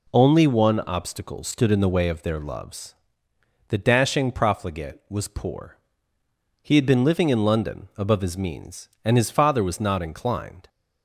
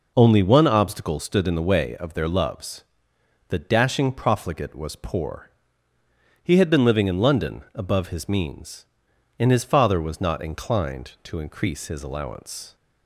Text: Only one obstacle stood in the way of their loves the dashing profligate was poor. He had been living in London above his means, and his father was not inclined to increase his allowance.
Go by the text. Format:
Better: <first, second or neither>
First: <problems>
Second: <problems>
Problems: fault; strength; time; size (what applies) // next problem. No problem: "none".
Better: second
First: pauses between "loves" and "the"; noticeable; at 2.9 s; 0.74 s long // stops before "to increase his allowance"; at 10.6 s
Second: pauses between "loves" and "the"; noticeable; at 2.8 s; 0.66 s long